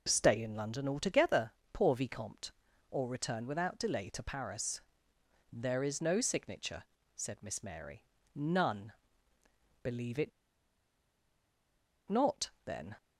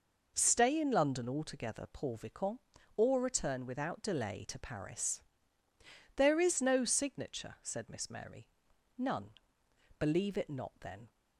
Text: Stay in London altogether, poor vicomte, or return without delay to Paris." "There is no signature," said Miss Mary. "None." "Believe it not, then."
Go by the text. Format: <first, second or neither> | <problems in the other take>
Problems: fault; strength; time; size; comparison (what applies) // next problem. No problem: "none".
second | pauses between "it" and "not"; strong; at 10.3 s; 1.7 s long